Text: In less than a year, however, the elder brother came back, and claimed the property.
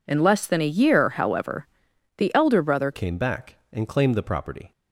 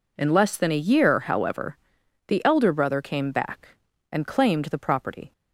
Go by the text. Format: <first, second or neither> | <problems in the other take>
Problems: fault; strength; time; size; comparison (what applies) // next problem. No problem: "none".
second | changes voice at "came"; from 2.9 s on; 1.8 s long